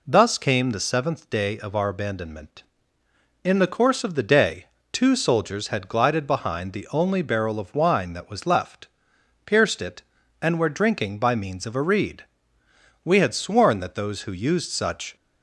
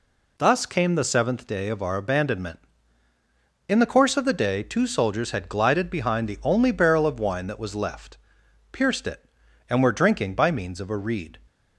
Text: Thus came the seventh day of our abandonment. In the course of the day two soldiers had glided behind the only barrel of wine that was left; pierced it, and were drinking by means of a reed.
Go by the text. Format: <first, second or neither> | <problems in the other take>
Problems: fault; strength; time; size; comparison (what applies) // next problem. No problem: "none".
second | pauses between "day" and "two"; slight; at 4.6 s; 0.26 s long // goes on to say "We had sworn that those who used such"; strong; from 13.0 s on; 2.1 s long